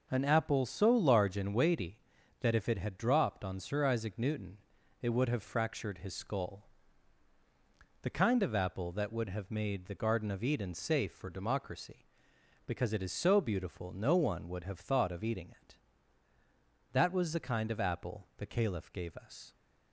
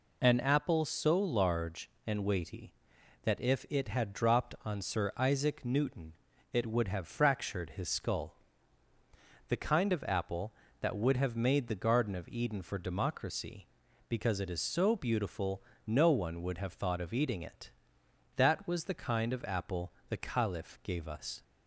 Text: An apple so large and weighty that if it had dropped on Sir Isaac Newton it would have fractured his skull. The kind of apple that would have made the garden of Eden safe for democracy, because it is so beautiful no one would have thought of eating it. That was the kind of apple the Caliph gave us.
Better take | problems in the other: first | pauses between "Newton" and "it"; at 6.1 s; 0.40 s long; also in the first // skips "safe"; at 12.6 s // pauses between "beautiful" and "no"; slight; at 15.6 s; 0.24 s long // pauses between "apple" and "the"; slight; at 19.9 s; 0.16 s long

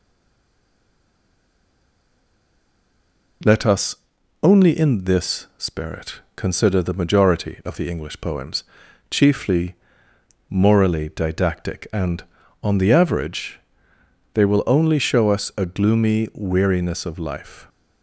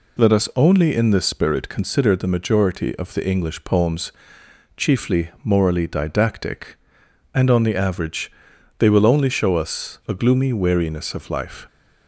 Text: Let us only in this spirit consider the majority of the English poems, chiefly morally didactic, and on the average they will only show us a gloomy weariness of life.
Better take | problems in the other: second | stays silent before the first word; strong; until 3.4 s; 3.4 s long // pauses between "us" and "only"; noticeable; at 3.9 s; 0.48 s long // pauses between "spirit" and "consider"; slight; at 6.2 s; 0.16 s long // pauses between "chiefly" and "morally"; noticeable; at 9.7 s; 0.74 s long // pauses between "average" and "they"; noticeable; at 13.5 s; 0.76 s long; noticeable in the second

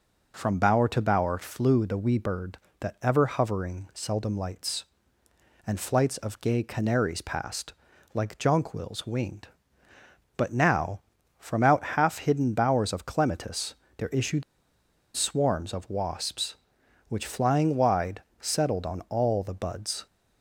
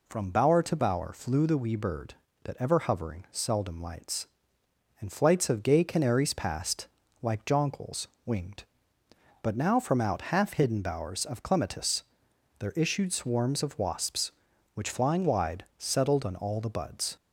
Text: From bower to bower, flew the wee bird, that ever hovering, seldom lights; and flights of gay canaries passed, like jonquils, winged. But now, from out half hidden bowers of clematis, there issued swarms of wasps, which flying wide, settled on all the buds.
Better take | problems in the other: second | pauses between "issued" and "swarms"; noticeable; at 14.4 s; 0.71 s long

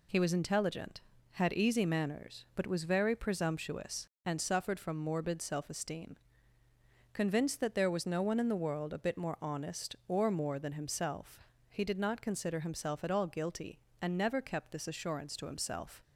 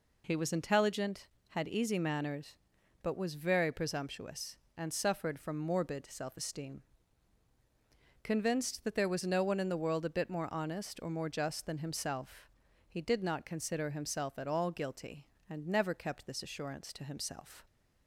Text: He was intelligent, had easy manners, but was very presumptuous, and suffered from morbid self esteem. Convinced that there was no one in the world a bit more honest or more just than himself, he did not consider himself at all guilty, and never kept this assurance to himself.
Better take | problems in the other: second | skips "just"; at 10.5 s

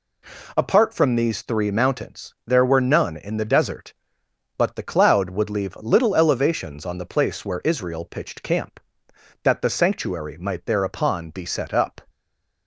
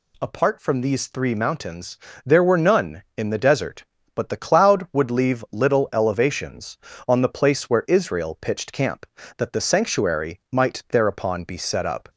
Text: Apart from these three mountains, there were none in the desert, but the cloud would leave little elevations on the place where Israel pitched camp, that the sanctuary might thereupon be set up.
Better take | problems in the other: second | stays silent after the last word; slight; from 12.0 s on; 0.6 s long

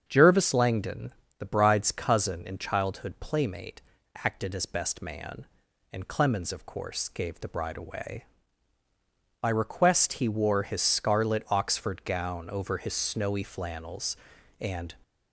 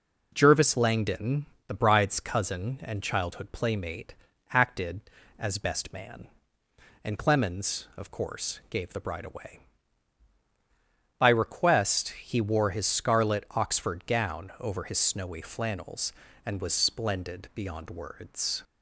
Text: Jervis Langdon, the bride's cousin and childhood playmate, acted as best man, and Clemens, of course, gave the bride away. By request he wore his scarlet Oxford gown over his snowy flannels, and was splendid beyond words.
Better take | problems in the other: second | starts louder than the rest; strong; until 1.0 s; 7.5 dB // stops before "was splendid beyond words"; at 15.0 s

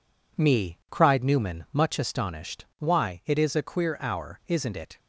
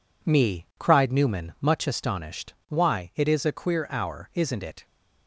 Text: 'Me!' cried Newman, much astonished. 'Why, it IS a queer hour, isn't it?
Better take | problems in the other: neither | none

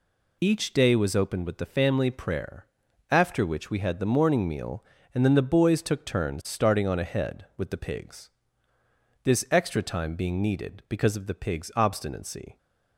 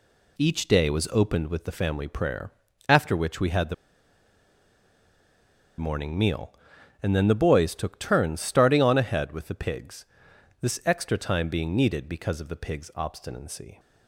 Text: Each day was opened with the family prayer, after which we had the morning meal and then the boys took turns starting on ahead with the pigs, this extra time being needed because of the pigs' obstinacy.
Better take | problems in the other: first | pauses between "the" and "morning"; strong; at 3.7 s; 2.0 s long

